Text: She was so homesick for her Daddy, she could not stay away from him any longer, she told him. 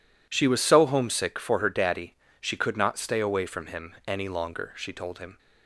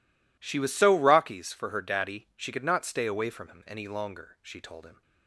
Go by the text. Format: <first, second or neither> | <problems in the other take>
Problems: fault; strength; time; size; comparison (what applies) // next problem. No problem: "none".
first | says "rockies" for "homesick"; at 0.9 s